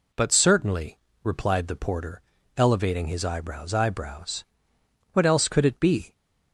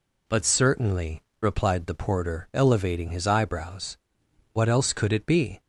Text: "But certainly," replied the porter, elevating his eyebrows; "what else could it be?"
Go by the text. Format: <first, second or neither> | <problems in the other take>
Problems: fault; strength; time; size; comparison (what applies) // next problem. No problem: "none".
second | says "eyebrows" twice; at 3.7 s